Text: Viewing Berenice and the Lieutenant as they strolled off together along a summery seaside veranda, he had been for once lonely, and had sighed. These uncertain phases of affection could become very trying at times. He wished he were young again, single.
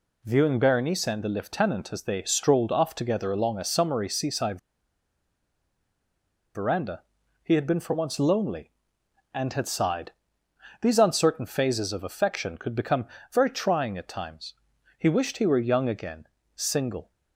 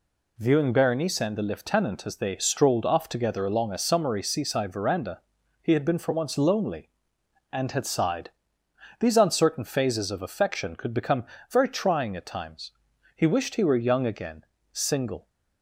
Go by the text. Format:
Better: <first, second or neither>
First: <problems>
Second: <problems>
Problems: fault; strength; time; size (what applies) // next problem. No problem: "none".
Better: second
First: pauses between "seaside" and "veranda"; strong; at 4.5 s; 1.9 s long // pauses between "become" and "very"; slight; at 13.0 s; 0.26 s long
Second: pauses between "become" and "very"; slight; at 11.2 s; 0.26 s long